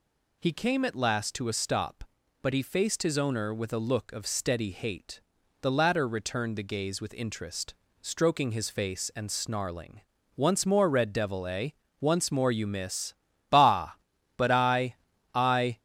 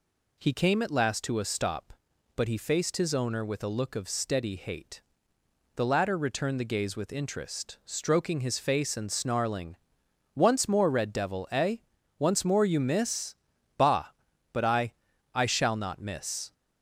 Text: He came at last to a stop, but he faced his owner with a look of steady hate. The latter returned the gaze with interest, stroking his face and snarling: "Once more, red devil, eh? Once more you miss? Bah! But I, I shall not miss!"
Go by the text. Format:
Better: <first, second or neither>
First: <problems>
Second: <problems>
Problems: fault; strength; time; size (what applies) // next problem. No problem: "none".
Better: second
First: stops before "shall not miss"; at 15.7 s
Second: none